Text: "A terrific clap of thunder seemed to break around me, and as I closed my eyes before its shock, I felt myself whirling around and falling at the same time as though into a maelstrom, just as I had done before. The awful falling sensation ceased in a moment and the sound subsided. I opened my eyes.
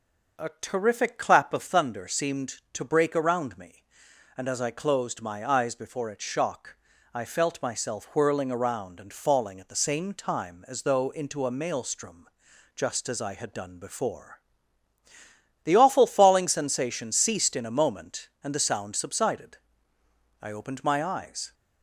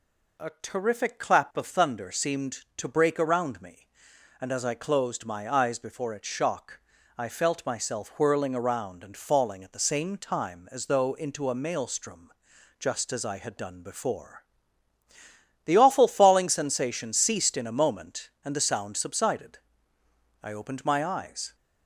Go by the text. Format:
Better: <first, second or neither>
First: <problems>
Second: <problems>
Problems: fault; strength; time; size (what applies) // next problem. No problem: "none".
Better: second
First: starts louder than the rest; noticeable; until 1.8 s; 6 dB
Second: none